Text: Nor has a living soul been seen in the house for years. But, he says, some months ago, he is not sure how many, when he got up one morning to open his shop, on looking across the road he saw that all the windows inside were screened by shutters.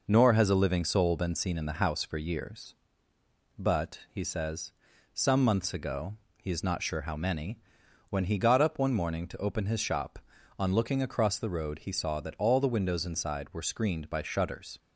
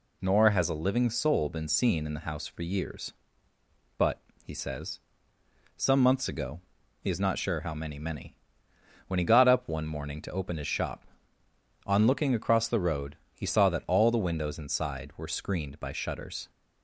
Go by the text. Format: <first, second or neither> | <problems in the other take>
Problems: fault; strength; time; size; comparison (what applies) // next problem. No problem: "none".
first | says "many" twice; at 7.9 s // pauses between "road" and "he"; slight; at 13.1 s; 0.18 s long